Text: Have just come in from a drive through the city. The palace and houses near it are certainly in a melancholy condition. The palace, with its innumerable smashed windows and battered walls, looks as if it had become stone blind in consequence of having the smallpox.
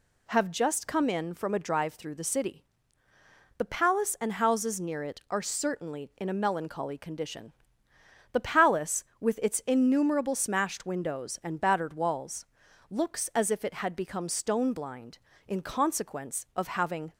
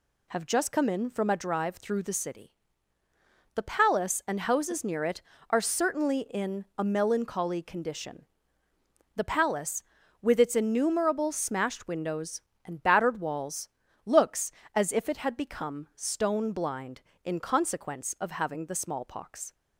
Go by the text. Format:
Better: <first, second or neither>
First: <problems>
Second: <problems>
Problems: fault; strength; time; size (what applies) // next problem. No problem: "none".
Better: second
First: stops before "the smallpox"; at 17.1 s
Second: none